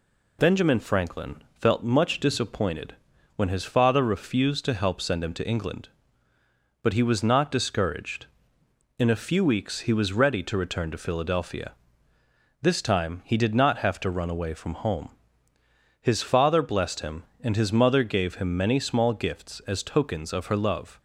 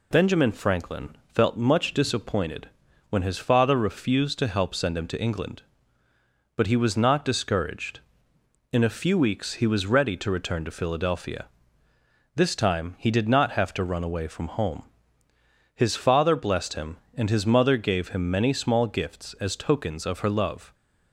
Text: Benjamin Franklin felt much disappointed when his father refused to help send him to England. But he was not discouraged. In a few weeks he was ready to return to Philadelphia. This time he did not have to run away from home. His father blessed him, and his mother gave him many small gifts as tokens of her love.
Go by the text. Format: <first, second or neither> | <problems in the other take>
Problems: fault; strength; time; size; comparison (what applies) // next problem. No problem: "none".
neither | pauses between "Franklin" and "felt"; slight; the same in both // pauses between "disappointed" and "when"; the same in both